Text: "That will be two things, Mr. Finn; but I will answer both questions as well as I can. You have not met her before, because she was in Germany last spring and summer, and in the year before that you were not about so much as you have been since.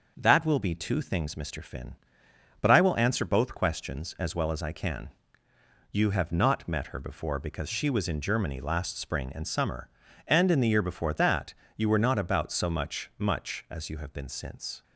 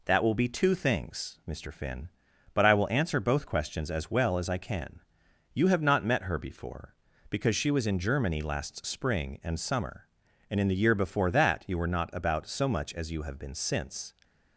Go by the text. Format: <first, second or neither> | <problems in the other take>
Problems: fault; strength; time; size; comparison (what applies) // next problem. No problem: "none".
second | starts louder than the rest; noticeable; until 1.1 s; 6 dB // pauses between "that" and "you"; slight; at 11.5 s; 0.22 s long // says "much" twice; at 13.1 s